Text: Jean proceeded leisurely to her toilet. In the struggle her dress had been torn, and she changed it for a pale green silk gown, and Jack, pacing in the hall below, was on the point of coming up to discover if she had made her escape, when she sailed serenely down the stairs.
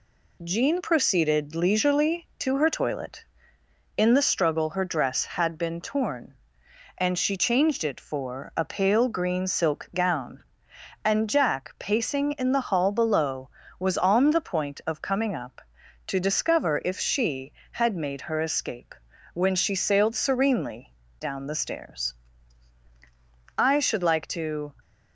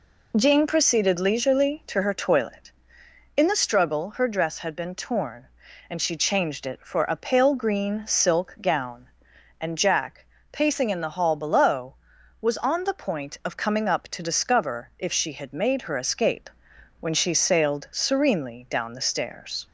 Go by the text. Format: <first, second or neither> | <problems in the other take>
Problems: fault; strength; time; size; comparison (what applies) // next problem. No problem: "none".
second | pauses between "serenely" and "down"; slight; at 20.9 s; 0.24 s long // goes on to say "I should like to"; noticeable; from 23.5 s on; 1.1 s long